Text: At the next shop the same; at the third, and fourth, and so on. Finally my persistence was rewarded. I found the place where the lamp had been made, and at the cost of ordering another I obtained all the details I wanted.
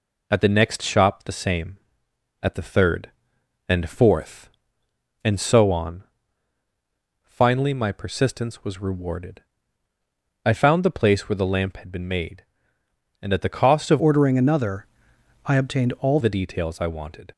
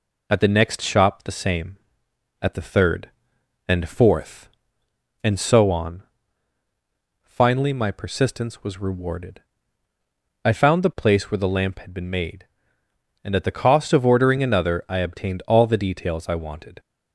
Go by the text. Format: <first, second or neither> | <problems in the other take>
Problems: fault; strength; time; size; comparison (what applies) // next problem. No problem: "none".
second | changes voice from "ordering" to "all"; from 13.9 to 16.1 s; 2.2 s long // pauses between "another" and "I"; noticeable; at 14.8 s; 0.58 s long